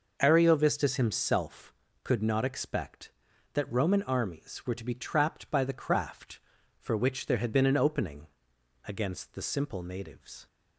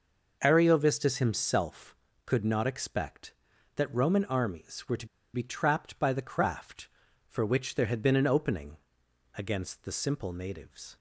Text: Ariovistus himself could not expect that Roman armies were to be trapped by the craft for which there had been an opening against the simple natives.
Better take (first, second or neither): first